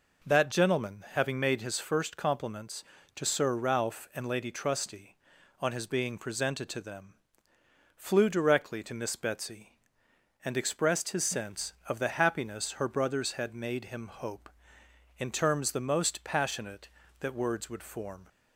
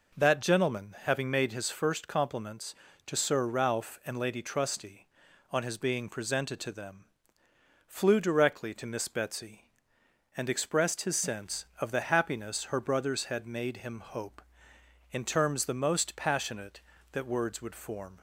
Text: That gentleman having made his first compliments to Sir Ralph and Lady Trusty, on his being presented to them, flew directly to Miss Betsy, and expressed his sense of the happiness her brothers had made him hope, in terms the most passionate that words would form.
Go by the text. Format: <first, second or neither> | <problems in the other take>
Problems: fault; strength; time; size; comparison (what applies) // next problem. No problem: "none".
neither | none